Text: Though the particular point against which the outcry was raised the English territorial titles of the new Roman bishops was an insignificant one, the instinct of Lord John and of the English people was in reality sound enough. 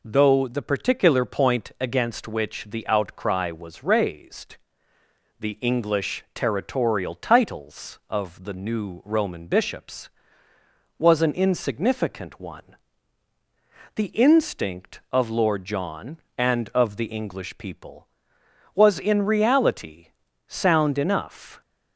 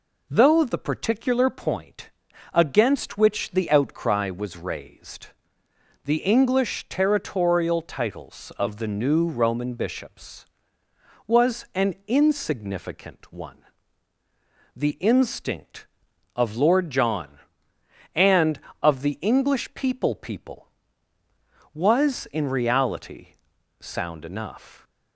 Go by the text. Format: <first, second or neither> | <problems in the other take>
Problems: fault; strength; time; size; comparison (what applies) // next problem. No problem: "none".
first | pauses between "point" and "against"; at 2.0 s; 0.42 s long // pauses between "raised" and "the"; noticeable; at 5.2 s; 0.76 s long; noticeable in the first // says "people" twice; at 20.1 s // pauses between "reality" and "sound"; noticeable; at 23.2 s; 0.52 s long; also in the first